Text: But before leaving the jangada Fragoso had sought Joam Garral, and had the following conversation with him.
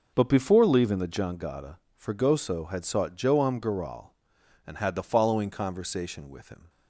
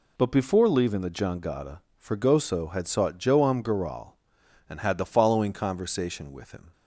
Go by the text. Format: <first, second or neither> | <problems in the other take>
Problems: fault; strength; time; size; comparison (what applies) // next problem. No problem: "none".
second | starts louder than the rest; noticeable; until 1.3 s; 5.5 dB // pauses between "jangada" and "Fragoso"; slight; at 1.7 s; 0.18 s long; slight in the second